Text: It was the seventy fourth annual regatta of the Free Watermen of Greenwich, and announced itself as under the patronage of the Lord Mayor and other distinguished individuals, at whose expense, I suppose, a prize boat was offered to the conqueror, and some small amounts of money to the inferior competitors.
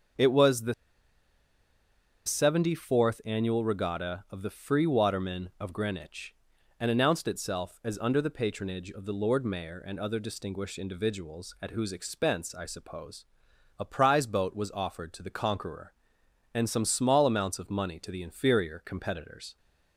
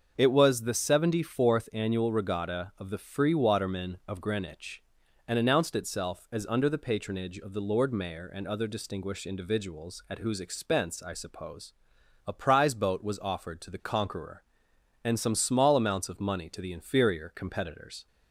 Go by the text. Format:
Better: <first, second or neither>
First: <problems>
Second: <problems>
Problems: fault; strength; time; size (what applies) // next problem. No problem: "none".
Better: second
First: starts louder than the rest; until 2.7 s; 6.5 dB // pauses between "the" and "seventy"; strong; at 0.7 s; 1.5 s long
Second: starts louder than the rest; until 1.1 s; 6.5 dB